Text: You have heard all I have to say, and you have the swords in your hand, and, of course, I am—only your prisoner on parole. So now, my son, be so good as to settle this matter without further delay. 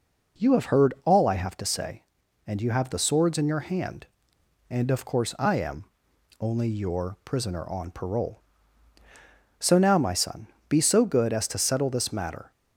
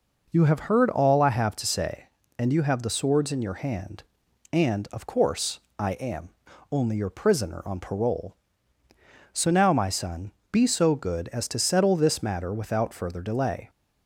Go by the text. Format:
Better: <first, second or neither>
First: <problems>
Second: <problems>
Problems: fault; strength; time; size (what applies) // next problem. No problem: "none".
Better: second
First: stops before "without further delay"; at 12.5 s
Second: none